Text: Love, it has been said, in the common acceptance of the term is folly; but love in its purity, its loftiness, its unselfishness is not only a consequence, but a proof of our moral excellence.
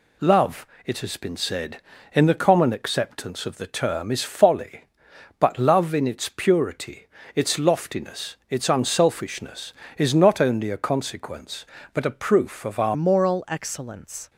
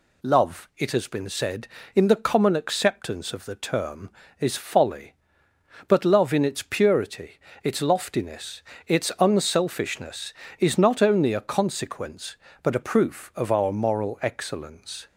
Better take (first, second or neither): second